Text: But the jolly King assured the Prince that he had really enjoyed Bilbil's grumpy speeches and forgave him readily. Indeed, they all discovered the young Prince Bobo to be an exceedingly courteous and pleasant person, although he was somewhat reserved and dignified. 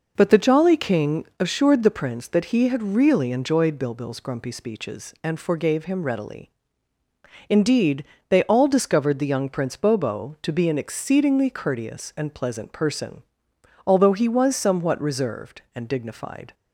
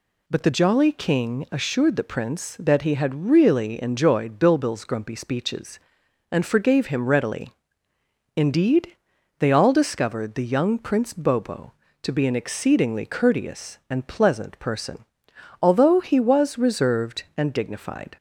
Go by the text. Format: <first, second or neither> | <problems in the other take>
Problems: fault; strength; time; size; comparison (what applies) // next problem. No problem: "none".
first | skips "somewhat"; at 16.5 s